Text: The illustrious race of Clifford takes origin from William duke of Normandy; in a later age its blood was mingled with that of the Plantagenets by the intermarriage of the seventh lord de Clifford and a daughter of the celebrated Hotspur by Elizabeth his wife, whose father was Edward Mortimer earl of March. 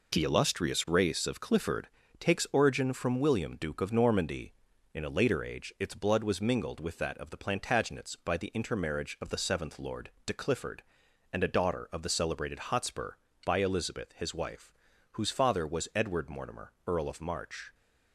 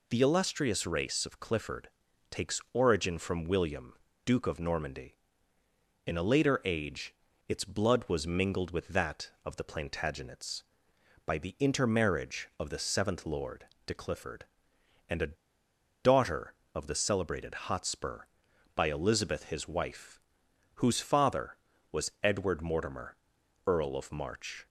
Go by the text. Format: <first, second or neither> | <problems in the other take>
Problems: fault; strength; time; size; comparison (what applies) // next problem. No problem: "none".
first | pauses between "Clifford" and "takes"; at 1.8 s; 0.42 s long; slight in the first // pauses between "William" and "duke"; slight; at 3.9 s; 0.30 s long // pauses between "age" and "its"; slight; at 7.1 s; 0.36 s long // pauses between "lord" and "de"; slight; at 13.6 s; 0.20 s long; slight in the first // pauses between "a" and "daughter"; noticeable; at 15.3 s; 0.67 s long // pauses between "celebrated" and "Hotspur"; slight; at 17.5 s; 0.16 s long // pauses between "Mortimer" and "earl"; noticeable; at 23.1 s; 0.52 s long; slight in the first